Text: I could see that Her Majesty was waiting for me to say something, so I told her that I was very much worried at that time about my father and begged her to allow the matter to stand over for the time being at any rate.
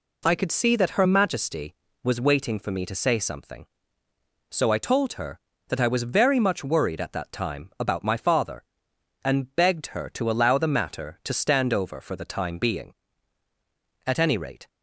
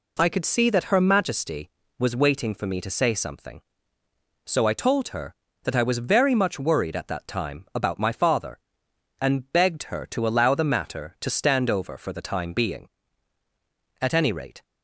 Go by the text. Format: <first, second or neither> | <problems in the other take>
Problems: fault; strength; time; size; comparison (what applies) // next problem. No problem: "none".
neither | none